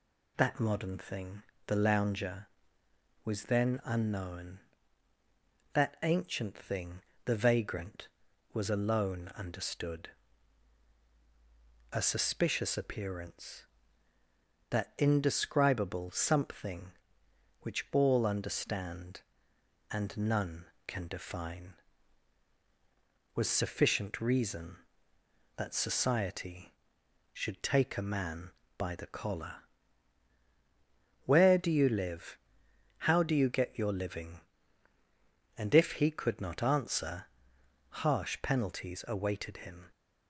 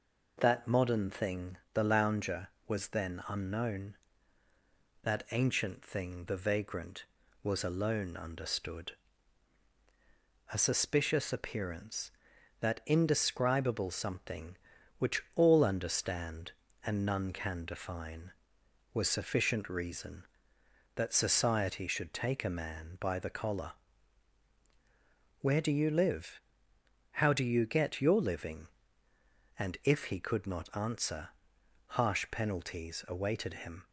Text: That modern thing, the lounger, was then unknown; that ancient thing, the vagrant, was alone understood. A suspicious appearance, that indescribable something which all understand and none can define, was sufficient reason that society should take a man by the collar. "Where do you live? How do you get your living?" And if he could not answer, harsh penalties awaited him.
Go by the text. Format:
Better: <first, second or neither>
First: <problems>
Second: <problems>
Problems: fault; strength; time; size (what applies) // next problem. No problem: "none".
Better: neither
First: none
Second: none